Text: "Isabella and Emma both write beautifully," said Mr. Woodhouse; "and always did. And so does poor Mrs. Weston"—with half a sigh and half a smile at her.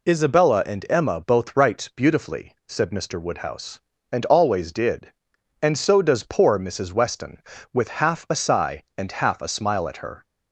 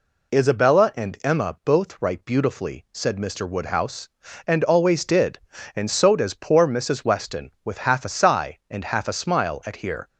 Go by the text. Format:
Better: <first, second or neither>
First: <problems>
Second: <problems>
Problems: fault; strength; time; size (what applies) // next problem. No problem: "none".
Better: first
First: none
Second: says "here" for "her"; at 9.7 s